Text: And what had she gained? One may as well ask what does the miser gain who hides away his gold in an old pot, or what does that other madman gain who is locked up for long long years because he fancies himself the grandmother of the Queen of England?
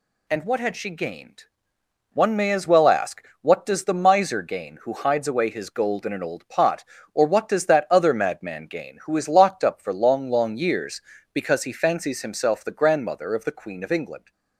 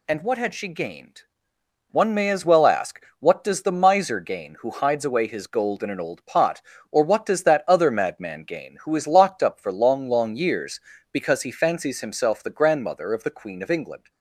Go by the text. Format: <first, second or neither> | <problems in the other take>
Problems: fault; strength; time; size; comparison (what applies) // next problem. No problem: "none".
neither | pauses between "ask" and "what"; slight; the same in both